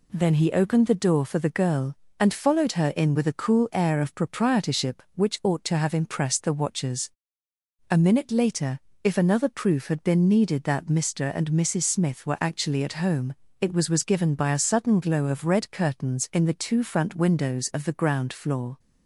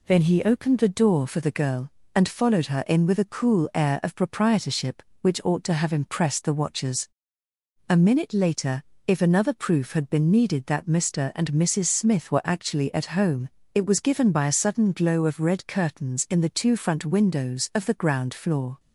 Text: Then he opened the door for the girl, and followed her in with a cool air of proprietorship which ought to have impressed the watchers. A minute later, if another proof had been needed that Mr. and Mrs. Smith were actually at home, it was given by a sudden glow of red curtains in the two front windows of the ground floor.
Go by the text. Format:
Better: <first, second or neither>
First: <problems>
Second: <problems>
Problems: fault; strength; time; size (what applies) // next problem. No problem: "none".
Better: second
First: says "was" twice; at 13.8 s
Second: none